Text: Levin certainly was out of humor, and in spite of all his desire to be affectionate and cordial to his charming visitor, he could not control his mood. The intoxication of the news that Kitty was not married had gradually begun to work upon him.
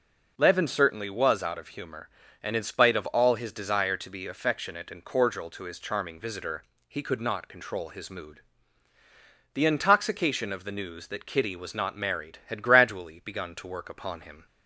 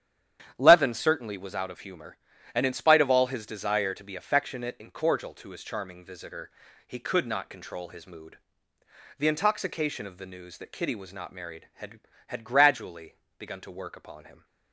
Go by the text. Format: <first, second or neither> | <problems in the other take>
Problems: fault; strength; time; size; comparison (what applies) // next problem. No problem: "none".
first | starts louder than the rest; strong; until 1.5 s; 9.5 dB // says "had" twice; at 12.2 s // pauses between "gradually" and "begun"; slight; at 13.1 s; 0.22 s long